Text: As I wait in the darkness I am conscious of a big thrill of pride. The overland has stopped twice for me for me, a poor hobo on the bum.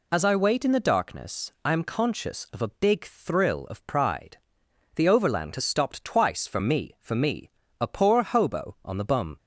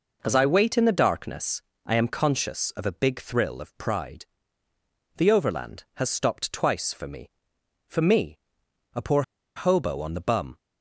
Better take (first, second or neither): first